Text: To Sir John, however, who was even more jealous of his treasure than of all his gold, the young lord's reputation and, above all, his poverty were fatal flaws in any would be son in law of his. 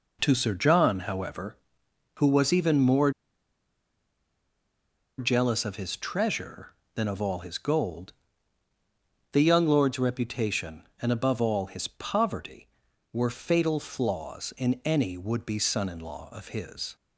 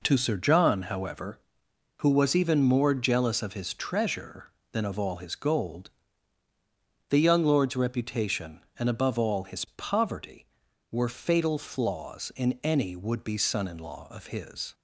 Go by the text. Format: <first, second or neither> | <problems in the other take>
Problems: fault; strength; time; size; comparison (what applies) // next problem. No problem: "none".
second | pauses between "more" and "jealous"; strong; at 3.0 s; 2.0 s long